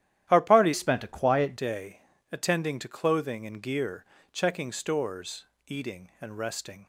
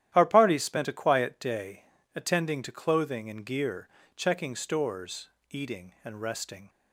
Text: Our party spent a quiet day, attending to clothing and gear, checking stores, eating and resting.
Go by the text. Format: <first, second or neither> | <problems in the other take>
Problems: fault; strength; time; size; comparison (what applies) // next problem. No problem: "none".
second | starts louder than the rest; strong; until 1.3 s; 11.5 dB; strong in the second // changes voice from "spent" to "quiet"; from 0.7 to 1.5 s; 0.8 s long